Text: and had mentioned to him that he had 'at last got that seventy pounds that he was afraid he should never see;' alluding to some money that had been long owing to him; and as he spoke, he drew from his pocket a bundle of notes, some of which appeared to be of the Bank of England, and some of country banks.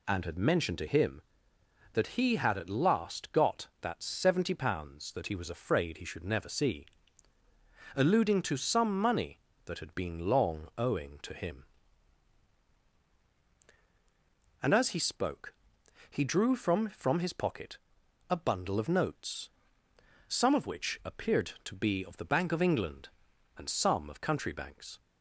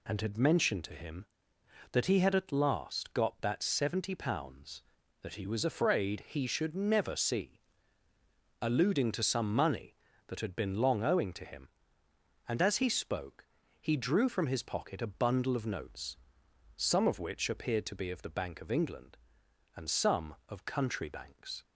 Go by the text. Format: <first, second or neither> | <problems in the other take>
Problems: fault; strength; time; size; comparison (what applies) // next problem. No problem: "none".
second | says "from" twice; at 16.8 s // pauses between "pocket" and "a"; noticeable; at 17.7 s; 0.52 s long